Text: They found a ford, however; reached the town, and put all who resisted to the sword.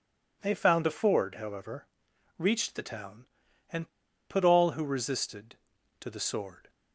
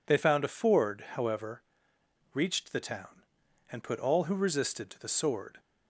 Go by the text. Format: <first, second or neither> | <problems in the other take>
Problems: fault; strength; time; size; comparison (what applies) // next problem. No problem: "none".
second | pauses between "and" and "put"; at 3.8 s; 0.41 s long